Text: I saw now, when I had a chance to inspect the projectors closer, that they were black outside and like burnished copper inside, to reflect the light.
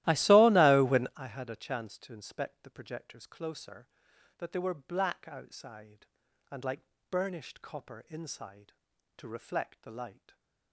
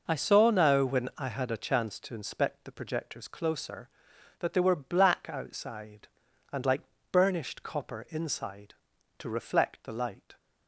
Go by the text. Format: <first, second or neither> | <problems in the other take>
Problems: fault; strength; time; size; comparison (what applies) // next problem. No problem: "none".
second | starts louder than the rest; strong; until 1.2 s; 15.5 dB // pauses between "like" and "burnished"; slight; at 6.8 s; 0.28 s long; slight in the second